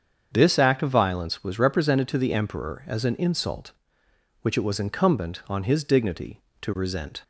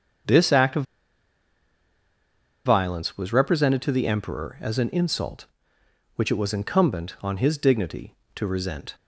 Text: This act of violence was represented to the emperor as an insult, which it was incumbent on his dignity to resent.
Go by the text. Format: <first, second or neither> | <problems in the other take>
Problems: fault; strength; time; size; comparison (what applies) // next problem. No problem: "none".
first | starts louder than the rest; strong; until 3.1 s; 7 dB; strong in the first // pauses between "of" and "violence"; strong; at 0.8 s; 1.8 s long